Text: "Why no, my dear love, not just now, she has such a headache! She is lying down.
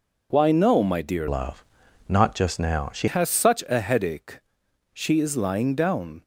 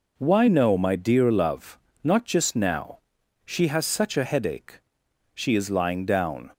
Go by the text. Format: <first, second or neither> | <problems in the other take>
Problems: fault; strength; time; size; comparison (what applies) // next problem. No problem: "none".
second | changes voice from "love" to "she"; from 1.2 to 3.0 s; 1.8 s long